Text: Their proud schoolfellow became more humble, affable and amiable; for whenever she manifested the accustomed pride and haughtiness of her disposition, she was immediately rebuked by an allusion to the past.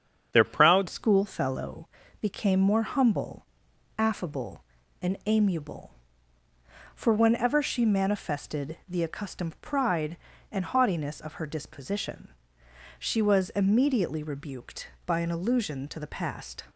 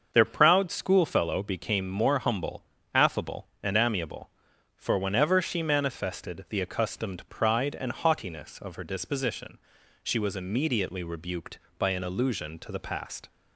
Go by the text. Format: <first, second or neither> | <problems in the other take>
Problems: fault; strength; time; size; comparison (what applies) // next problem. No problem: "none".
second | starts louder than the rest; strong; until 1.3 s; 7.5 dB; also in the second // changes voice at "schoolfellow"; from 0.8 s on; 15.8 s long // pauses between "schoolfellow" and "became"; slight; at 1.8 s; 0.36 s long